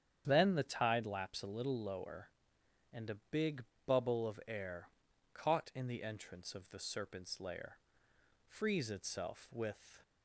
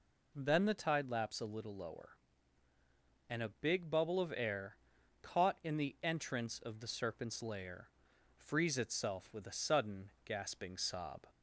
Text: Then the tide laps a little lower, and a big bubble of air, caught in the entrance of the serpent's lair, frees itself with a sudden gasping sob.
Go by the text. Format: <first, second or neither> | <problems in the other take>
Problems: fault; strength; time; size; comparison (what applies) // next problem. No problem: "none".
second | starts louder than the rest; strong; until 1.2 s; 9 dB // pauses between "big" and "bubble"; slight; at 3.6 s; 0.24 s long // stops before "a sudden gasping sob"; at 10.0 s